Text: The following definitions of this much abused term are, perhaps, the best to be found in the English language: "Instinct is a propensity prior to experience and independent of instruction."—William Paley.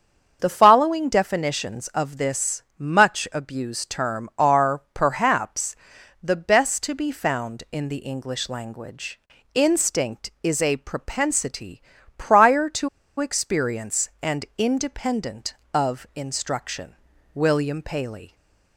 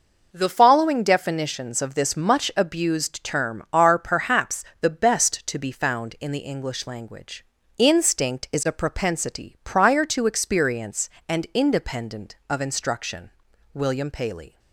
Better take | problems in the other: second | starts louder than the rest; until 1.4 s; 7 dB // pauses between "this" and "much"; slight; at 2.6 s; 0.16 s long // pauses between "propensity" and "prior"; slight; at 11.8 s; 0.34 s long // pauses between "to" and "experience"; slight; at 12.8 s; 0.30 s long // stays silent after the last word; slight; from 18.2 s on; 0.5 s long

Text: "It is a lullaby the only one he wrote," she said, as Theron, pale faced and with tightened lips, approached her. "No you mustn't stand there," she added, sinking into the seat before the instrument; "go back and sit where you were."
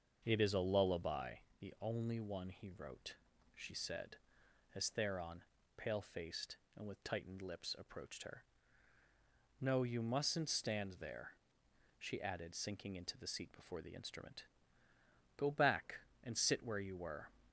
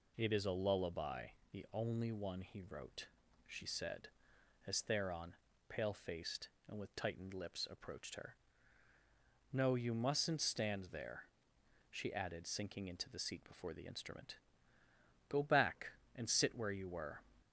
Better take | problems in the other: second | starts louder than the rest; until 1.3 s; 6.5 dB // pauses between "lullaby" and "the"; slight; at 1.3 s; 0.22 s long; slight in the second

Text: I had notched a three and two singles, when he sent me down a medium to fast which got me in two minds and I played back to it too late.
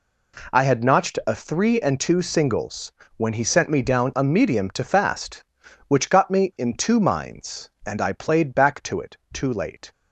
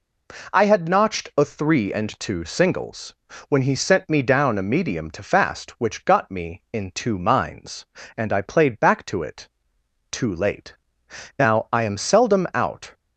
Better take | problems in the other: first | pauses between "it" and "too"; noticeable; at 9.4 s; 0.62 s long; slight in the first // goes on to say "Now I am seldom out"; from 11.3 s on; 1.5 s long

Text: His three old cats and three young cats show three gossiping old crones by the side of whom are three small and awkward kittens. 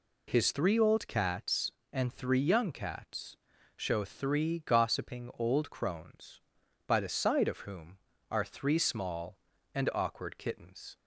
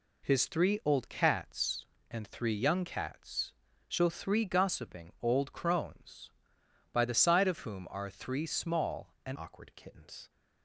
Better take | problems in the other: first | pauses between "cats" and "show"; at 3.5 s; 0.38 s long; also in the first // changes voice at "awkward"; from 9.3 s on; 0.9 s long

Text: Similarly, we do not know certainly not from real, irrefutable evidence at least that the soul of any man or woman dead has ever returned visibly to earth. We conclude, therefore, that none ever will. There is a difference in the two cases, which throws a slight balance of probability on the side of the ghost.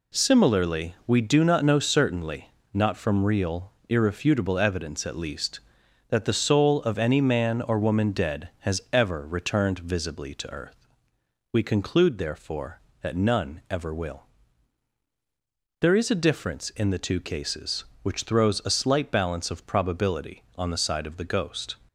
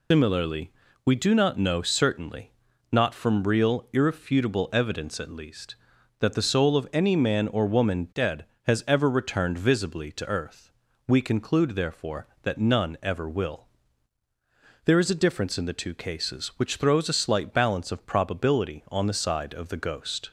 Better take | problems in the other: first | loses the start of "Similarly"; at 0.1 s; 140 ms // pauses between "certainly" and "not"; at 2.5 s; 0.40 s long; slight in the first

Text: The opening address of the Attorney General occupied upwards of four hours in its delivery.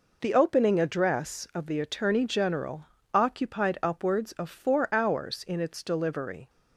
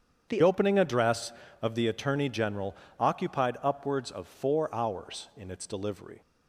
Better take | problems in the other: first | starts louder than the rest; strong; until 1.3 s; 8 dB // changes voice at "opening"; from 0.4 s on; 5.8 s long // pauses between "General" and "occupied"; slight; at 2.7 s; 0.24 s long; slight in the first

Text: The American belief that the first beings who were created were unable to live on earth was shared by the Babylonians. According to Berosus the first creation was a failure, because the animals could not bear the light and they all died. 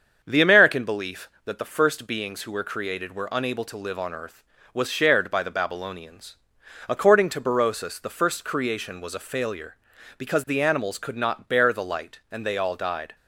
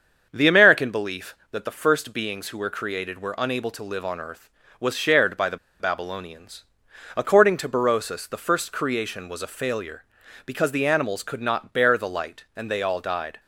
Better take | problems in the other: first | starts louder than the rest; strong; until 1.3 s; 7 dB; strong in the first // pauses between "the" and "Babylonians"; slight; at 5.5 s; 0.23 s long

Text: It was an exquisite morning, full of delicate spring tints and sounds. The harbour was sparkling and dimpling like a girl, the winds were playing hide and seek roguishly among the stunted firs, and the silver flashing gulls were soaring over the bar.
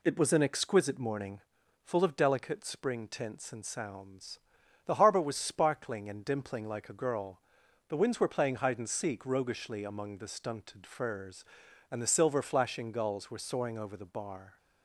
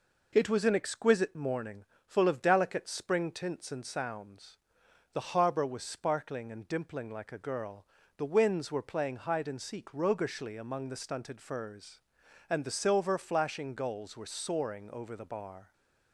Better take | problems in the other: neither | none

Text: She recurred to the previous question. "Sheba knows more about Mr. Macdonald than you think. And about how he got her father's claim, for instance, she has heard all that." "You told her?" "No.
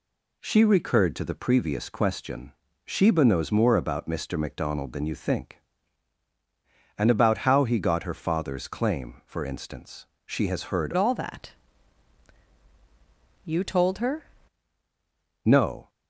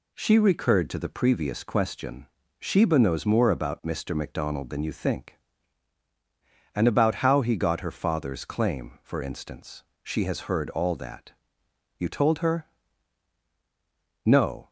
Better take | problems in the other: second | changes voice from "all" to "her"; from 10.9 to 14.2 s; 3.3 s long

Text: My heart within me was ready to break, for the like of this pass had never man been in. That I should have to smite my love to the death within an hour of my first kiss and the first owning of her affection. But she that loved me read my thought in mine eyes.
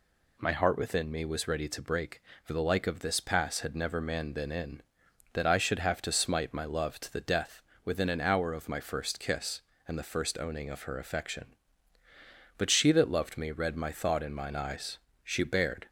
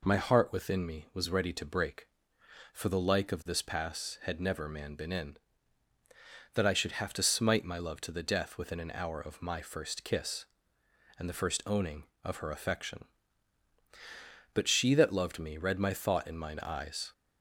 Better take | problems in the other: second | pauses between "death" and "within"; slight; at 7.6 s; 0.22 s long // goes on to say "She bared"; noticeable; from 15.2 s on; 0.64 s long

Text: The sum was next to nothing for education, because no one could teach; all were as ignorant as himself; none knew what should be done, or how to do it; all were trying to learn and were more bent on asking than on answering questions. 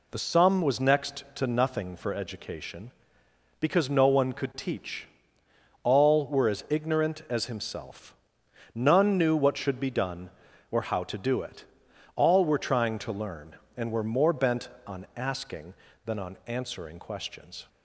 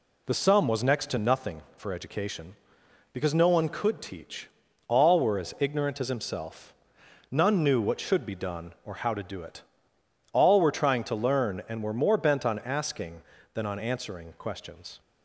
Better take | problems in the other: neither | none

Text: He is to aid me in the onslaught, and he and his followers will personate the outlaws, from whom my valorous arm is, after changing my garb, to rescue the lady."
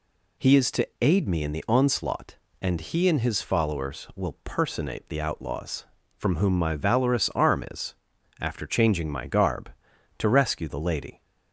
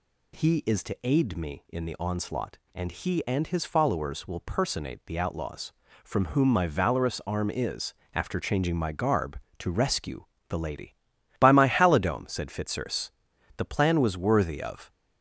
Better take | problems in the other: first | pauses between "rescue" and "the"; slight; at 10.2 s; 0.24 s long // goes on to say "By my halidome said Fitzurse the plan was worthy of"; strong; from 11.3 s on; 3.5 s long

